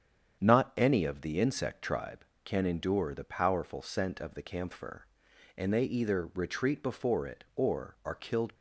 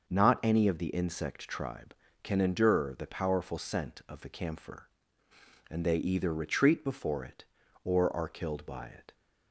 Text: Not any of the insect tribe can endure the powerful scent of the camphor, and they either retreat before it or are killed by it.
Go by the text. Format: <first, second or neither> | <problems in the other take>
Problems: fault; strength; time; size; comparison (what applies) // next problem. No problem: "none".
second | starts louder than the rest; strong; until 1.4 s; 8 dB; noticeable in the second // stops before "by it"; at 8.5 s